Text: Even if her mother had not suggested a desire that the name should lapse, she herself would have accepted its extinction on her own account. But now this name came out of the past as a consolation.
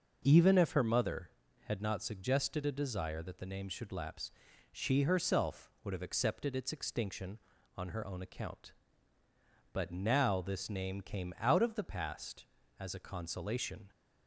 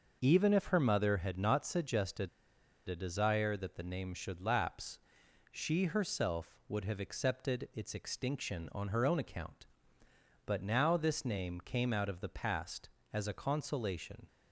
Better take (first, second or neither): first